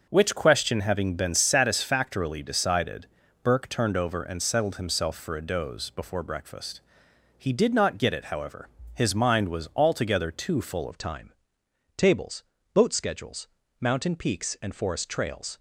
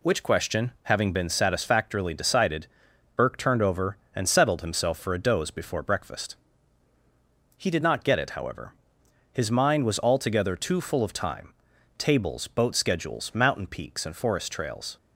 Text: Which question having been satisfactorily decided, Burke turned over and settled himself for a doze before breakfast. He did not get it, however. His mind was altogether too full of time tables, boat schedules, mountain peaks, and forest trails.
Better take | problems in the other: second | changes voice at "of"; from 10.9 s on; 4.6 s long // pauses between "time" and "tables"; noticeable; at 11.3 s; 0.64 s long; noticeable in the second

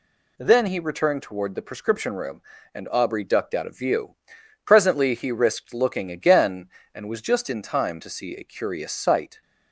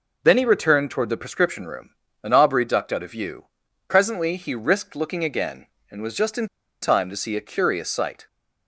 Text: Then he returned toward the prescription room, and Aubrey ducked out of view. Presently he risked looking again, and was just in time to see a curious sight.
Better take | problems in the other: first | pauses between "in" and "time"; slight; at 6.4 s; 0.35 s long

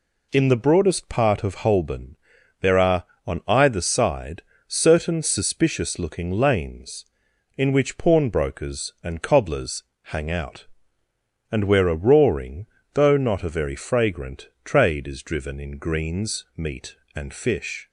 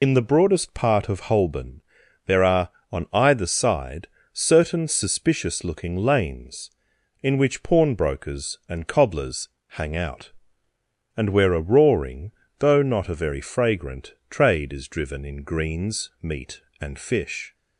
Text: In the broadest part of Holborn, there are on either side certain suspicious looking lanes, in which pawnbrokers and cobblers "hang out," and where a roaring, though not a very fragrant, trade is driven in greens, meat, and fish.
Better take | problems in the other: first | loses the start of "In"; at 0.0 s; 60 ms // pauses between "side" and "certain"; slight; at 4.0 s; 0.24 s long; slight in the first // pauses between "cobblers" and "hang"; slight; at 9.4 s; 0.18 s long; slight in the first

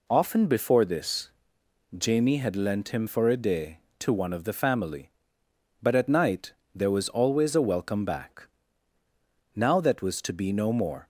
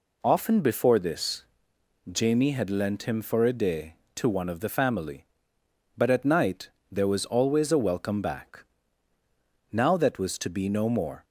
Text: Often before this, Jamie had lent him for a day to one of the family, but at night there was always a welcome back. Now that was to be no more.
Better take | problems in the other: neither | pauses between "night" and "there"; slight; the same in both

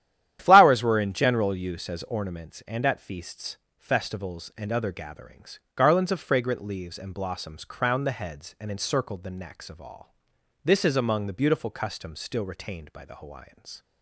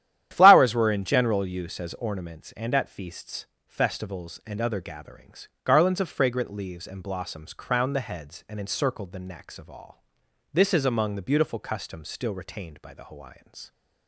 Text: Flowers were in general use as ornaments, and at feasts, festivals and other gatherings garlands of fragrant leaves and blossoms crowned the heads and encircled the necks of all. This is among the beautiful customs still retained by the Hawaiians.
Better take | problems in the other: neither | starts louder than the rest; strong; the same in both // pauses between "gatherings" and "garlands"; slight; the same in both

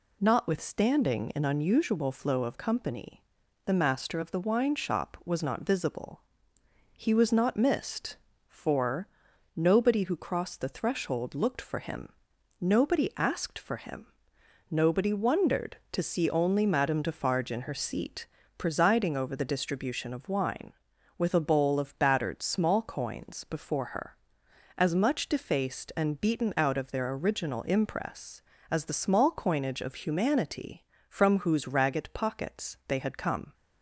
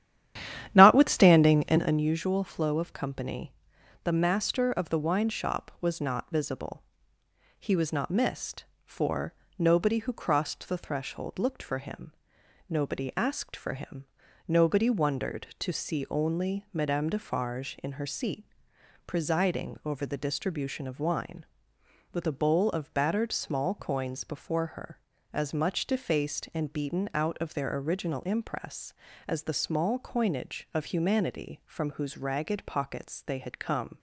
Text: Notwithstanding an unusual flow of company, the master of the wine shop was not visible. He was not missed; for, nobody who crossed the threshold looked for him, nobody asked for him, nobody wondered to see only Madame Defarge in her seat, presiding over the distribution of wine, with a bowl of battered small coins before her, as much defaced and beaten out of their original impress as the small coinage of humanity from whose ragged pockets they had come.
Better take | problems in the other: first | starts louder than the rest; strong; until 2.0 s; 11 dB

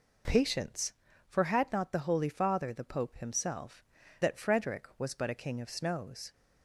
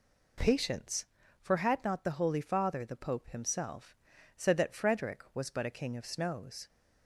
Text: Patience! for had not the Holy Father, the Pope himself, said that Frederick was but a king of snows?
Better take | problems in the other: second | skips "said"; at 4.0 s

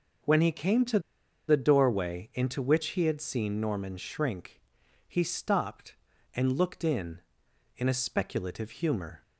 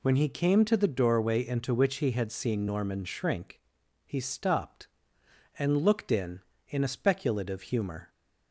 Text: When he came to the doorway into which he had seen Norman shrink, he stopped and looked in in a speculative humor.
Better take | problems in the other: second | pauses between "to" and "the"; noticeable; at 0.9 s; 0.48 s long

